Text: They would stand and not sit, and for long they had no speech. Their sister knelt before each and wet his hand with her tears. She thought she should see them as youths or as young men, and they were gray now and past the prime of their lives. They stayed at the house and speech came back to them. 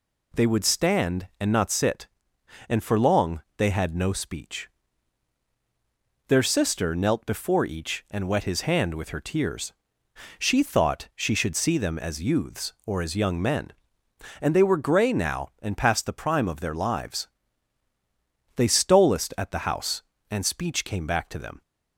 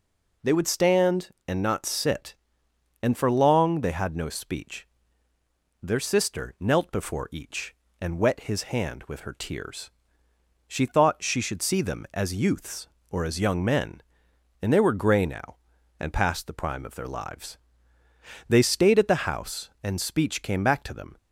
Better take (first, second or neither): second